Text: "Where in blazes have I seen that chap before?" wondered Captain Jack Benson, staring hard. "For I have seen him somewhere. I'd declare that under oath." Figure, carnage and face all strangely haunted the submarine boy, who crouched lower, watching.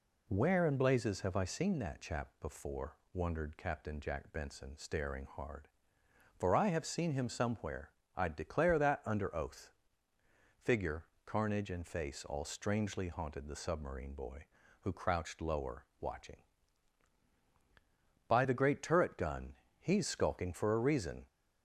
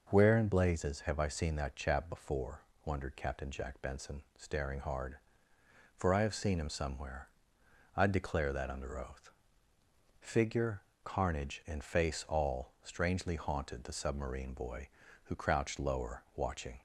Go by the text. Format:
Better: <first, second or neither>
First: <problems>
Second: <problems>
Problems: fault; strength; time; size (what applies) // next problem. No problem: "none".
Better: second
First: goes on to say "By the great turret gun He's skulking for a reason"; strong; from 18.2 s on; 2.9 s long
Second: none